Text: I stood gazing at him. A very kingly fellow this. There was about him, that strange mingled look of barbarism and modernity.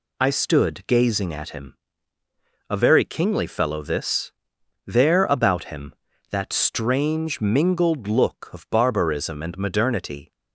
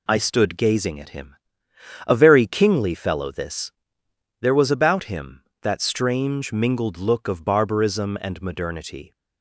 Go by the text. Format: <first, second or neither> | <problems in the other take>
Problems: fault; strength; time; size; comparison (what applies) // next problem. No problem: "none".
second | skips "was"; at 5.2 s